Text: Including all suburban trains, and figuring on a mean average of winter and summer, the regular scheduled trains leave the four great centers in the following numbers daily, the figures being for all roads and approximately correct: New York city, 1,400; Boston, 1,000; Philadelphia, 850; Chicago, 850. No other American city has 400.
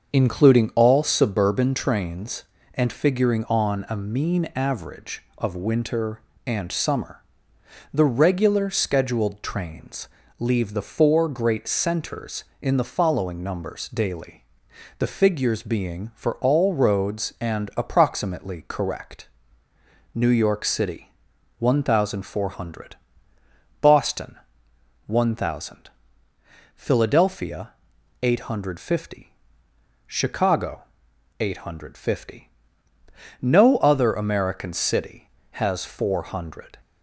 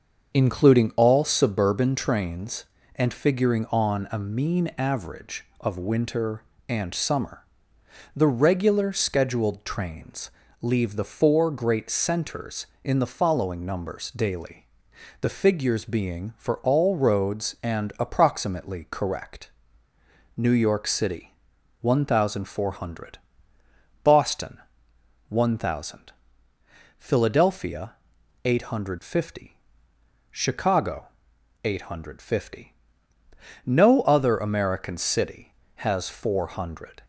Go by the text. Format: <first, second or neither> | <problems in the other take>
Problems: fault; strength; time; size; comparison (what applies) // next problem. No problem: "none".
neither | starts louder than the rest; the same in both // pauses between "trains" and "leave"; slight; the same in both